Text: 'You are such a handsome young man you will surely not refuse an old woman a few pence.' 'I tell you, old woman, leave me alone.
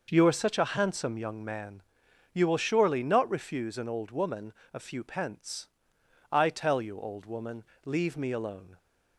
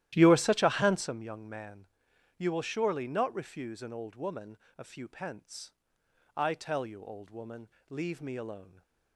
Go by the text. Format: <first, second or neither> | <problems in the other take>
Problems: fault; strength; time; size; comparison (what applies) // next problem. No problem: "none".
first | starts louder than the rest; strong; until 1.1 s; 13 dB // pauses between "man" and "you"; noticeable; at 1.8 s; 0.48 s long; noticeable in the first // pauses between "woman" and "a"; slight; at 4.5 s; 0.20 s long; slight in the first